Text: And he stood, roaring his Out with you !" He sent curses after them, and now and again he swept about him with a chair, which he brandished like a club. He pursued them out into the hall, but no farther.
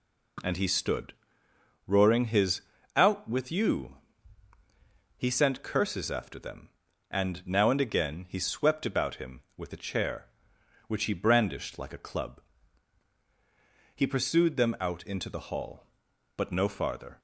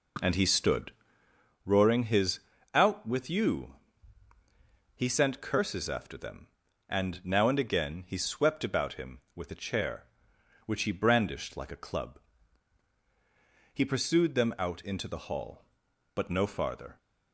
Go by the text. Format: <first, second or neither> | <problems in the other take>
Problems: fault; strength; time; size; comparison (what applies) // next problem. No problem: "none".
first | starts louder than the rest; noticeable; until 1.5 s; 4.5 dB // pauses between "his" and "Out"; slight; at 2.3 s; 0.34 s long; slight in the first